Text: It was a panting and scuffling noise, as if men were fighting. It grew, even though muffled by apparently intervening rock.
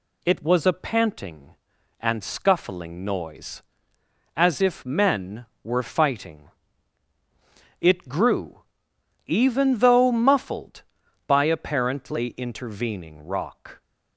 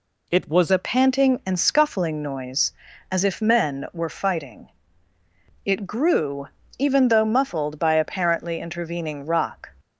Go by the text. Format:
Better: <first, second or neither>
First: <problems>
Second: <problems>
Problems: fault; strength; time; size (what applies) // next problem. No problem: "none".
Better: first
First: none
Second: changes voice at "a"; from 0.7 s on; 8.9 s long